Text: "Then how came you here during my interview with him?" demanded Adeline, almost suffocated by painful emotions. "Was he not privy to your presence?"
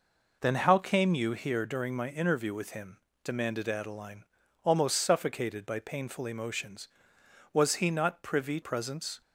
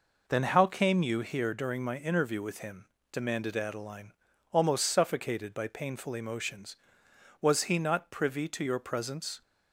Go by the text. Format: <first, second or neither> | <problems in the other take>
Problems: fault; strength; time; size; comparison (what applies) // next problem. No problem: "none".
second | skips "to your"; at 8.6 s